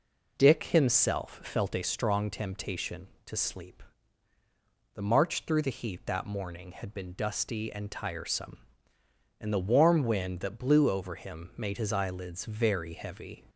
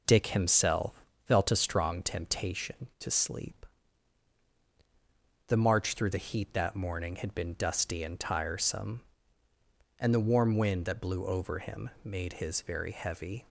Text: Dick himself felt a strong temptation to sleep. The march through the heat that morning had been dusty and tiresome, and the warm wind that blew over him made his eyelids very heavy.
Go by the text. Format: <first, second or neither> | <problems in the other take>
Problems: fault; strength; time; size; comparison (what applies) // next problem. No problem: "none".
first | pauses between "himself" and "felt"; slight; at 1.0 s; 0.24 s long // skips "eyelids"; at 12.6 s